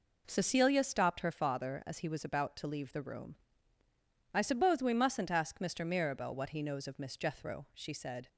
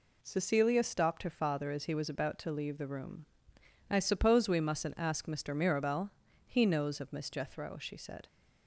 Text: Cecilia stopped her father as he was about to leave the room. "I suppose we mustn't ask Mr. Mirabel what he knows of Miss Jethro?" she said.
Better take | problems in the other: first | skips "what"; at 6.2 s

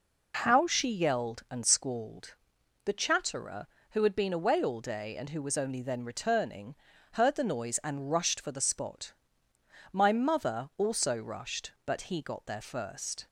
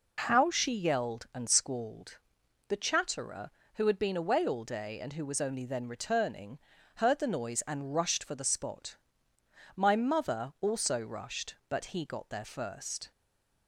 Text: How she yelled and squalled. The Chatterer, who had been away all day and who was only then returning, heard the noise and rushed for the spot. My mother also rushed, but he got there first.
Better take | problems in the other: first | stays silent after the last word; slight; from 13.1 s on; 0.5 s long

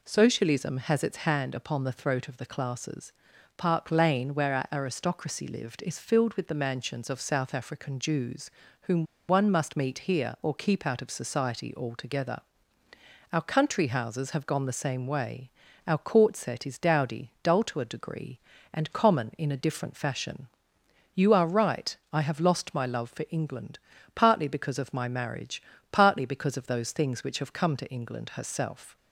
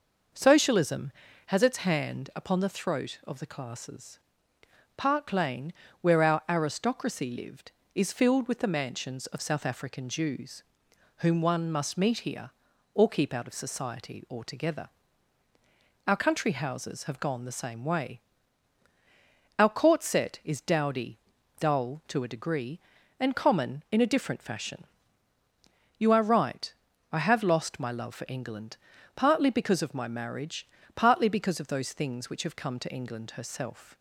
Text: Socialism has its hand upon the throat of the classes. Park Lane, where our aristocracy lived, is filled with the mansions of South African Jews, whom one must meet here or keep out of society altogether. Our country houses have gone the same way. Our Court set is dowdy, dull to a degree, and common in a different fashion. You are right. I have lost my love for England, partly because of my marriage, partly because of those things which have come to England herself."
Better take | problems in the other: second | pauses between "whom" and "one"; slight; at 9.0 s; 0.25 s long

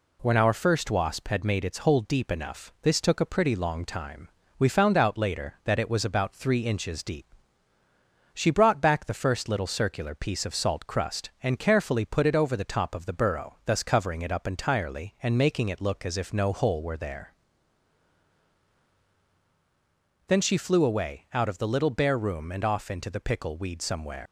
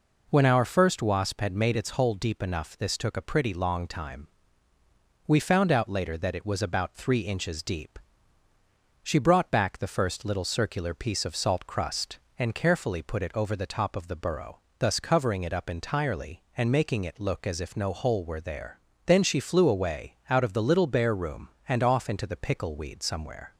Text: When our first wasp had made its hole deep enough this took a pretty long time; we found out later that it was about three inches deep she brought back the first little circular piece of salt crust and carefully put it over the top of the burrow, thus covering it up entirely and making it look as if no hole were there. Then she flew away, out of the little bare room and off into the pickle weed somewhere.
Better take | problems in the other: second | pauses between "deep" and "she"; at 7.2 s; 1.1 s long; also in the second // leaves "somewhere" unfinished; at 24.2 s; 110 ms

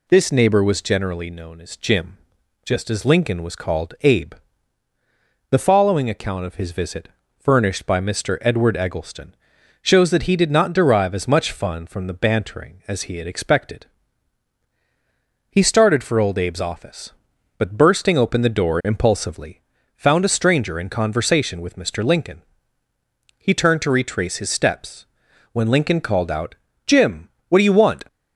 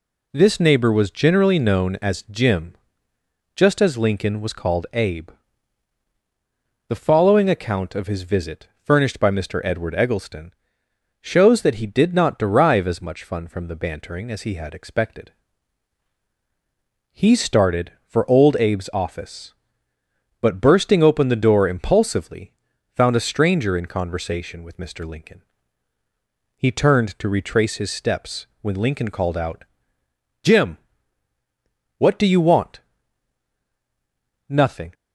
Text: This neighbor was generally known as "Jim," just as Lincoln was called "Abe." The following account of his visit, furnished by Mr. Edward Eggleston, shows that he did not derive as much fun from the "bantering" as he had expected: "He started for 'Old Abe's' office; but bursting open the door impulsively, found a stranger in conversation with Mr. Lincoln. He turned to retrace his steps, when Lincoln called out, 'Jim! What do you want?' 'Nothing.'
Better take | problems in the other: second | stops before "Nothing"; at 28.0 s

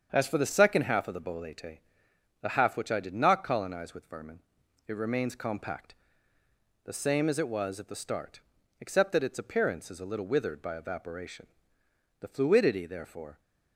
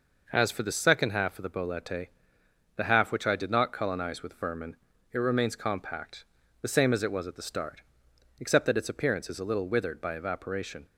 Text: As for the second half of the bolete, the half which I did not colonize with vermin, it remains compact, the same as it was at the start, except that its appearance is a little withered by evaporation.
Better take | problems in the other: second | starts louder than the rest; strong; until 1.1 s; 7.5 dB // goes on to say "The fluidity therefore"; noticeable; from 12.1 s on; 1.2 s long

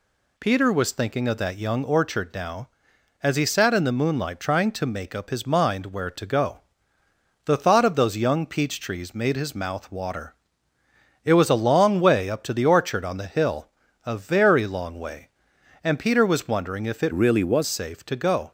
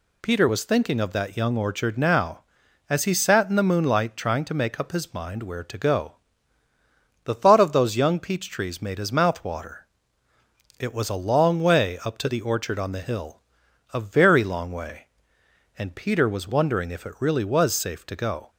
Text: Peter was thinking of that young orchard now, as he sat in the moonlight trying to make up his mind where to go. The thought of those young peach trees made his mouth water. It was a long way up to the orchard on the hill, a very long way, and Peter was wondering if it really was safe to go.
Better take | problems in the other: second | changes voice from "really" to "was"; from 17.1 to 17.6 s; 0.5 s long

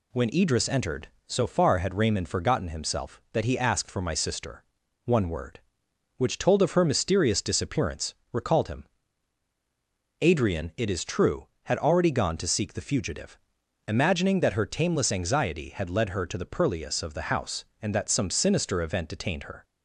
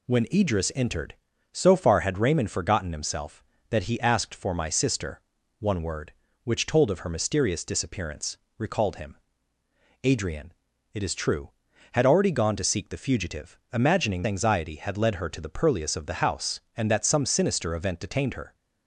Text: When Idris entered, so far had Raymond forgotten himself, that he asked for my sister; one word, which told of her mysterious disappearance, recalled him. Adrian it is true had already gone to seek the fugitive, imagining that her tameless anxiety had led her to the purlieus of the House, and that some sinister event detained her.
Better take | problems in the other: first | pauses between "Adrian" and "it"; at 10.5 s; 0.40 s long // skips "that her tameless"; at 14.2 s

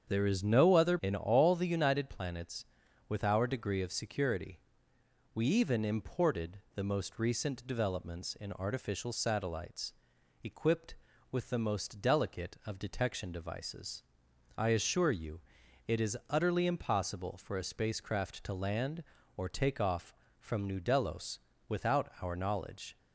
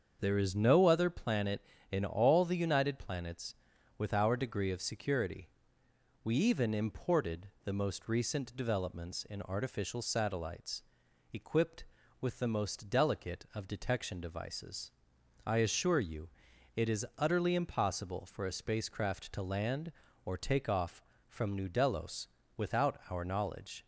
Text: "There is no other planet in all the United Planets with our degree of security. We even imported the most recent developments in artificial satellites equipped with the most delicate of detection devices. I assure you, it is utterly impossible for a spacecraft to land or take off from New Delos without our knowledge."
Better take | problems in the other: second | starts louder than the rest; strong; until 1.1 s; 7.5 dB; also in the second // skips "planet"; at 0.9 s // pauses between "imported" and "the"; slight; at 6.5 s; 0.16 s long; slight in the second // pauses between "satellites" and "equipped"; noticeable; at 9.9 s; 0.50 s long; noticeable in the second // pauses between "Delos" and "without"; slight; at 21.3 s; 0.30 s long; slight in the second

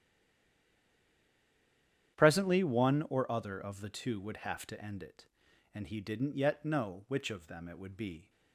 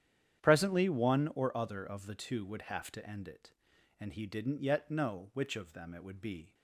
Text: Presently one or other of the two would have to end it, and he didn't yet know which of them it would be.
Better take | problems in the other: second | stays silent before the first word; until 2.1 s; 2.1 s long // starts louder than the rest; strong; until 3.2 s; 10 dB; strong in the second

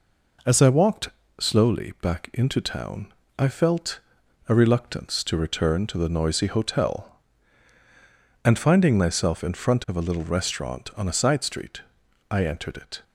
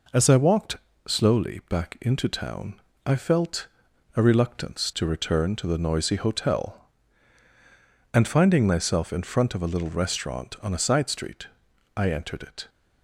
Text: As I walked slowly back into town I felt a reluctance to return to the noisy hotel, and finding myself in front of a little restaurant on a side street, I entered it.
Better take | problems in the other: neither | pauses between "walked" and "slowly"; slight; the same in both // pauses between "town" and "I"; slight; the same in both // pauses between "felt" and "a"; noticeable; the same in both

